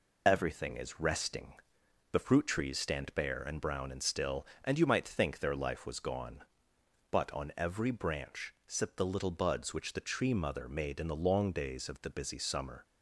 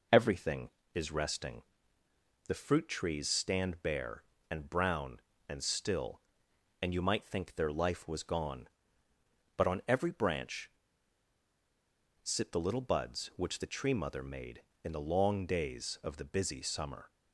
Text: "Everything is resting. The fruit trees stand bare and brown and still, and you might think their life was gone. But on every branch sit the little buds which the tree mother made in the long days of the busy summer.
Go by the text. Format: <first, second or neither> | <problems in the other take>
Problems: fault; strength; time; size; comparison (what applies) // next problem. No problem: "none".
first | pauses between "branch" and "sit"; strong; at 10.7 s; 1.5 s long